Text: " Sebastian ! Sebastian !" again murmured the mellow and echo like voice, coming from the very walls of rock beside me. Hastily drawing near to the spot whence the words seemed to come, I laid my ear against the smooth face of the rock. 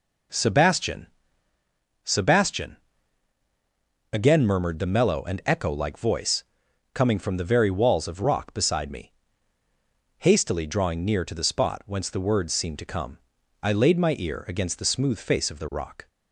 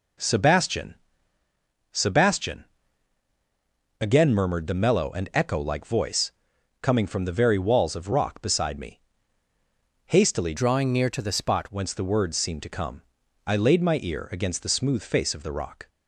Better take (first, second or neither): first